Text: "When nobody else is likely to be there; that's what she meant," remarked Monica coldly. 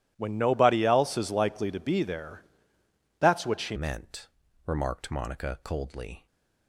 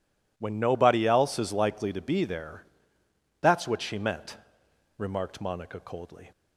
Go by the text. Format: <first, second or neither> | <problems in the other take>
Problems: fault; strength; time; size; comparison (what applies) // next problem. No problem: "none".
second | changes voice at "meant"; from 3.7 s on; 2.5 s long